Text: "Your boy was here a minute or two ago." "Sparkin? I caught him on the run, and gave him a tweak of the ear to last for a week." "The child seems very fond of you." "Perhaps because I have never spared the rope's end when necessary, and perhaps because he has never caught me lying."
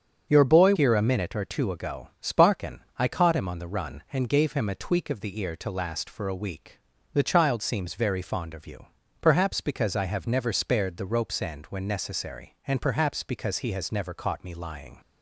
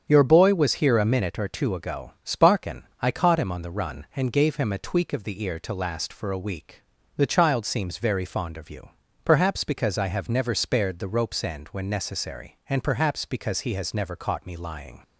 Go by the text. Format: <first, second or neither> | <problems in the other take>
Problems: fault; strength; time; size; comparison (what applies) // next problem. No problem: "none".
second | starts louder than the rest; until 1.3 s; 6.5 dB; strong in the second // skips "was"; at 0.7 s